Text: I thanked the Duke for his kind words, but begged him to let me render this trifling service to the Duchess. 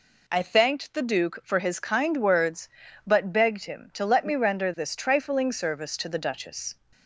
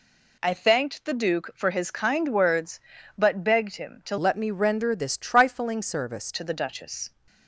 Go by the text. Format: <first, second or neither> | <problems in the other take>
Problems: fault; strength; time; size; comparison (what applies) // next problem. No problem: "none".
first | changes voice from "let" to "service"; from 4.1 to 6.3 s; 2.2 s long